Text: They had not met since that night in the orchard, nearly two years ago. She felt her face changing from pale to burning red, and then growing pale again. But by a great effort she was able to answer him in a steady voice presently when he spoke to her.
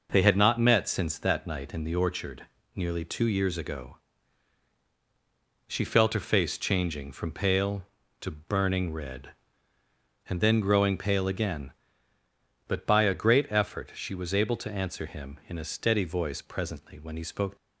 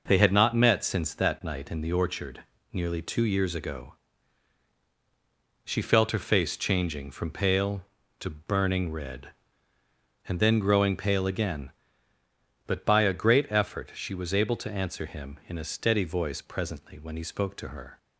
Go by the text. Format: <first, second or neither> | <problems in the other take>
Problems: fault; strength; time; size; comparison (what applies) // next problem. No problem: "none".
second | stops before "to her"; at 17.5 s